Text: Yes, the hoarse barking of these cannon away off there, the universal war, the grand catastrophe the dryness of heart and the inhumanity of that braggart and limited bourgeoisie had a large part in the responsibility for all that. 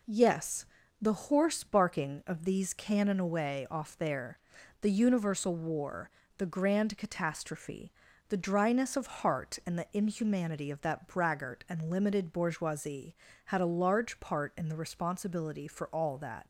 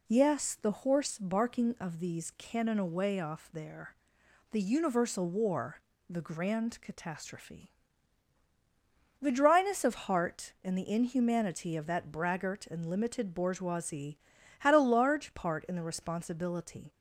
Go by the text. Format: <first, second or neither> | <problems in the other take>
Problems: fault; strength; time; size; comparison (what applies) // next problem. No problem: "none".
first | pauses between "catastrophe" and "the"; strong; at 7.7 s; 1.4 s long; also in the first // stops before "for all that"; at 16.9 s